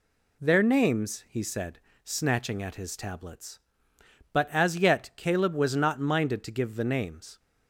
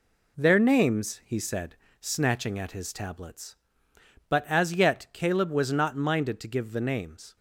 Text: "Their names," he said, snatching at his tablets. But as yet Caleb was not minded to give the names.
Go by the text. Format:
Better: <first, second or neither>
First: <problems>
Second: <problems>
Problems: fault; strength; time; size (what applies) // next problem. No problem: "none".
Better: first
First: none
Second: gets quieter; noticeable; throughout; 5.5 dB